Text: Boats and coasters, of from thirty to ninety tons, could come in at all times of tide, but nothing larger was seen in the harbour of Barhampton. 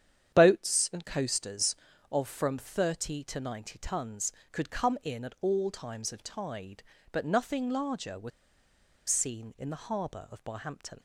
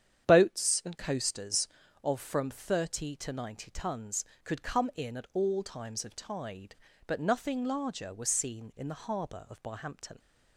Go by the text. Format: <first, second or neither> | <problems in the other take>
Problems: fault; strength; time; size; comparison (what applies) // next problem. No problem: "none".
second | starts louder than the rest; strong; until 1.3 s; 9 dB; strong in the second // pauses between "was" and "seen"; noticeable; at 8.3 s; 0.79 s long